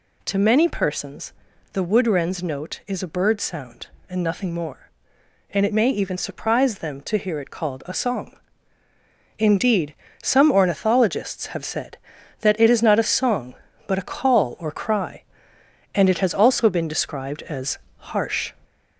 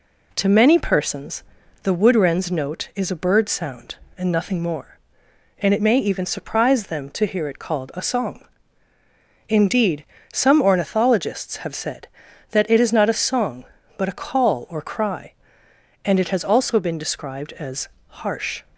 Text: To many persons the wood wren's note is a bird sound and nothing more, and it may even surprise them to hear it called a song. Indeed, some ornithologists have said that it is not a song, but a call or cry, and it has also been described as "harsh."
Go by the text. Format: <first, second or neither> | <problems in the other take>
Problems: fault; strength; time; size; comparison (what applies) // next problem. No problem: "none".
second | gets louder; throughout; 3.5 dB // pauses between "persons" and "the"; at 1.3 s; 0.40 s long; also in the second // pauses between "as" and "harsh"; slight; at 17.7 s; 0.20 s long; slight in the second